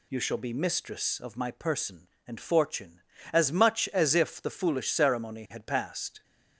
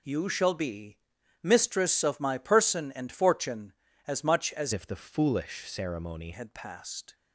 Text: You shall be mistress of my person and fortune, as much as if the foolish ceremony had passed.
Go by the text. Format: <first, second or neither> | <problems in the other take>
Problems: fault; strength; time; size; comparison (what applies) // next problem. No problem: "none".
first | pauses between "be" and "mistress"; at 0.9 s; 0.44 s long // changes voice from "if" to "ceremony"; from 4.7 to 6.3 s; 1.6 s long